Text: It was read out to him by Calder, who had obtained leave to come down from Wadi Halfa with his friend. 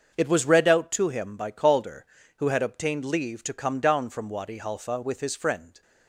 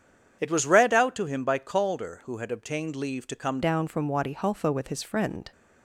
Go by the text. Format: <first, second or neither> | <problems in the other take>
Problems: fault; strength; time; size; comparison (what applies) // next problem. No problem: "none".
first | starts louder than the rest; strong; until 1.4 s; 8 dB; also in the first // changes voice at "down"; from 3.6 s on; 1.9 s long